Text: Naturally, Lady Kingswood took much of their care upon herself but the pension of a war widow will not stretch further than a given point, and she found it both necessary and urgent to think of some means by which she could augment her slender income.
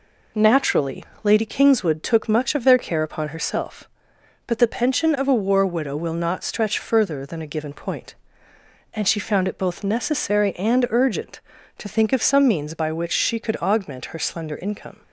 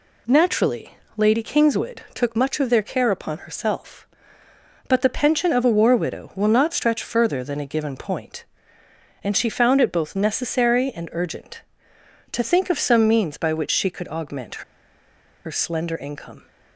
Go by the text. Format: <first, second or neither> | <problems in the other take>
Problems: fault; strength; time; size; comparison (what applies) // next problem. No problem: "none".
first | pauses between "augment" and "her"; noticeable; at 14.6 s; 0.83 s long